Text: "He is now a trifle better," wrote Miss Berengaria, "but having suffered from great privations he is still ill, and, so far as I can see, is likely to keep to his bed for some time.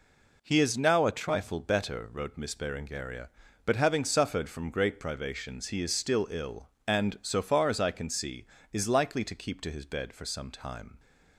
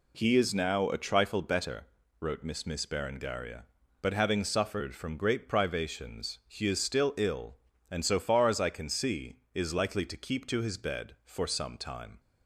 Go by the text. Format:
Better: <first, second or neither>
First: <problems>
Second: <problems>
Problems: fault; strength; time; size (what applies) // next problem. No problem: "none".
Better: first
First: none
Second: says "Miss" twice; at 2.6 s